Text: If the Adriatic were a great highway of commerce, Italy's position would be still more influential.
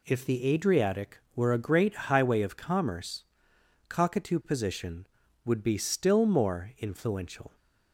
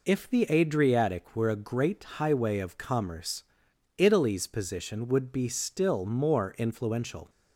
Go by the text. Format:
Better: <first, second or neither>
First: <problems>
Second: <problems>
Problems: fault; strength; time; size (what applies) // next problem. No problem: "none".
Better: second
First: says "Cockatoo" for "Italy's"; at 3.8 s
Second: none